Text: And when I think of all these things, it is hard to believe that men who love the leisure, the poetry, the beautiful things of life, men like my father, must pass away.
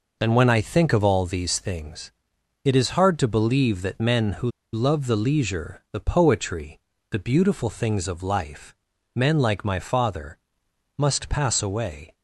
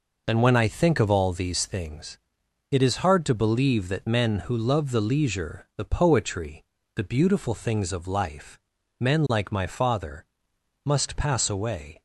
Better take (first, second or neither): second